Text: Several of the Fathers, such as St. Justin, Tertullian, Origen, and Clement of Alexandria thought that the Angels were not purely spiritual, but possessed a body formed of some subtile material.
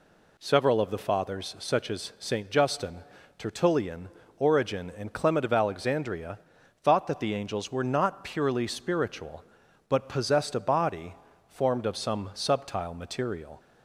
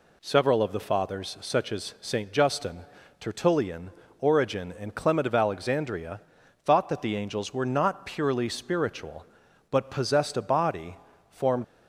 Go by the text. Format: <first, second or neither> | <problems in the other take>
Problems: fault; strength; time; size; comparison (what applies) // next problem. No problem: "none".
first | pauses between "Alexandria" and "thought"; noticeable; at 6.1 s; 0.46 s long; noticeable in the first // pauses between "body" and "formed"; slight; at 10.9 s; 0.32 s long; slight in the first // stops before "of some subtile material"; at 11.6 s